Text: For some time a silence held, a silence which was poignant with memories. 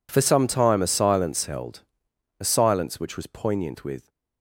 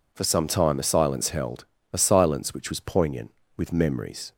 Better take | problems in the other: second | stops before "memories"; at 4.0 s

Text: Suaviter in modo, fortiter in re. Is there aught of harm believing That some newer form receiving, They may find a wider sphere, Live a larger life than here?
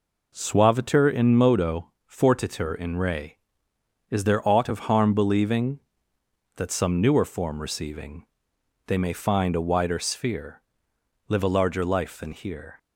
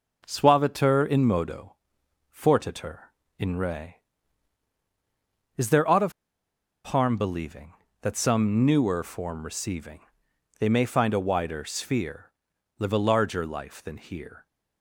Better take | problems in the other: first | pauses between "of" and "harm"; noticeable; at 6.1 s; 0.73 s long

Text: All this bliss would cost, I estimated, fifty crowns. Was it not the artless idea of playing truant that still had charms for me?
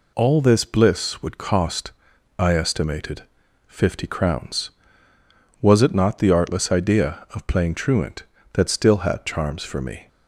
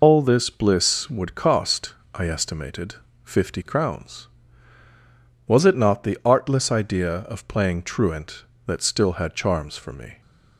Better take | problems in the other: first | loses the start of "All"; at 0.0 s; 145 ms

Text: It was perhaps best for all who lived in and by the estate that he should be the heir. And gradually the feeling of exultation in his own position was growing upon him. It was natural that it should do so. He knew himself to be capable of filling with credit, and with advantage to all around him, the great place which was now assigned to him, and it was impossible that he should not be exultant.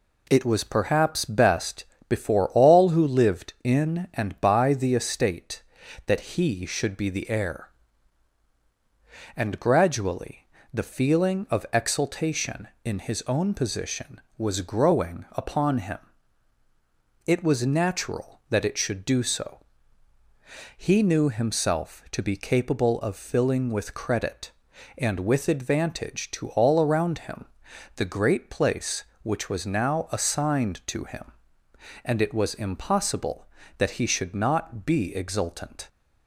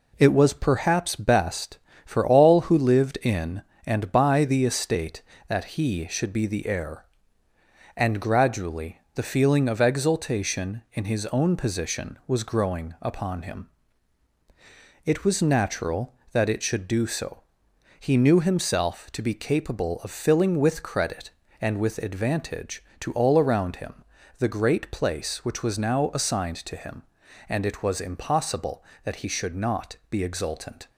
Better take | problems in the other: second | says "before" for "for"; at 2.0 s // pauses between "gradually" and "the"; slight; at 10.4 s; 0.26 s long; slight in the second

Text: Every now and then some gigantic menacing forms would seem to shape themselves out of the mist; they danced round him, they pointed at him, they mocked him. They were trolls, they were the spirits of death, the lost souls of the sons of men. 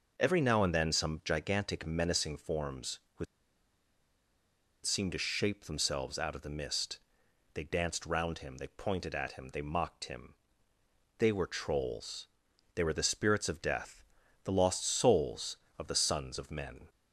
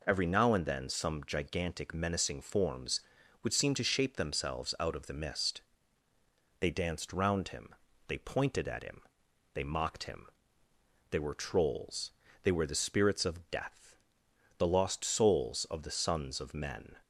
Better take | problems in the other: second | pauses between "would" and "seem"; strong; at 3.2 s; 1.6 s long

